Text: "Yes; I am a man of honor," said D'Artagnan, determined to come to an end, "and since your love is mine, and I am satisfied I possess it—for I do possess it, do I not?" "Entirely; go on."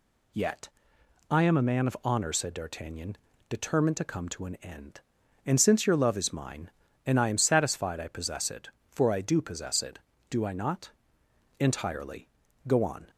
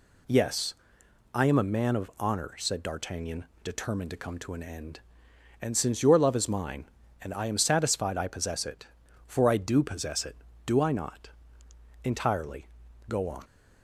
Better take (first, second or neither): second